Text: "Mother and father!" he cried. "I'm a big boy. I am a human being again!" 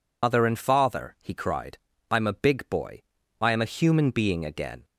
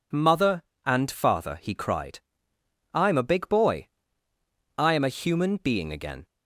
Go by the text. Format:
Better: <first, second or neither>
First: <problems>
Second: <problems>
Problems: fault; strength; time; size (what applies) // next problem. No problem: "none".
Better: second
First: loses the start of "Mother"; at 0.2 s; 80 ms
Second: none